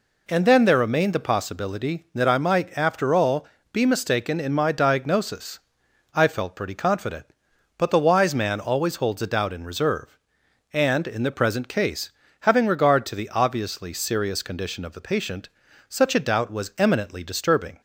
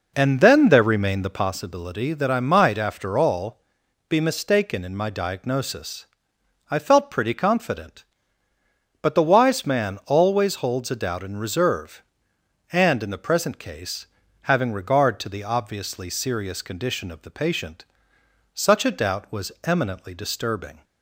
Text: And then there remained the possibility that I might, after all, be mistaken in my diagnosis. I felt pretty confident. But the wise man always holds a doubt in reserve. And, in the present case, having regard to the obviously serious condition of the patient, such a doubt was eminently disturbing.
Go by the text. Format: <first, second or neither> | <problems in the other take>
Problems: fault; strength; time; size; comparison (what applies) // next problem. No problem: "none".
first | starts louder than the rest; noticeable; until 1.5 s; 4.5 dB